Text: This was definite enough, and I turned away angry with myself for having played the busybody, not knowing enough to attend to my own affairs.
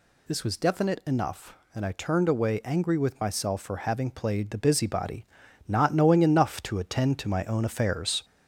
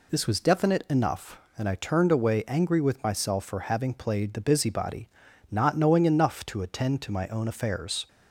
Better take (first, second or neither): second